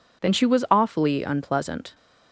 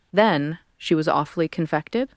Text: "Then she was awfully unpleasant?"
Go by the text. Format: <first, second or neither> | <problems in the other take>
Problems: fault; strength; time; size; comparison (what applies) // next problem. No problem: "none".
first | pauses between "Then" and "she"; slight; at 0.5 s; 0.20 s long // says "confected" for "unpleasant"; at 1.4 s